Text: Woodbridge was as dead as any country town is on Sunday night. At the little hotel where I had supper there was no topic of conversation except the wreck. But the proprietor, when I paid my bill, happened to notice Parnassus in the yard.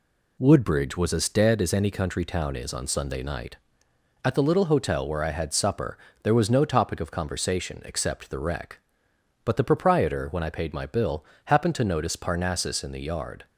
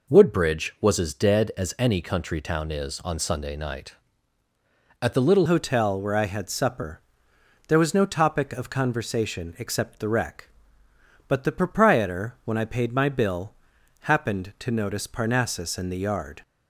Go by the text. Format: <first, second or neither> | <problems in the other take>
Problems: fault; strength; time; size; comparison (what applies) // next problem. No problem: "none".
first | changes voice at "hotel"; from 5.4 s on; 11.0 s long // pauses between "supper" and "there"; noticeable; at 6.9 s; 0.68 s long; slight in the first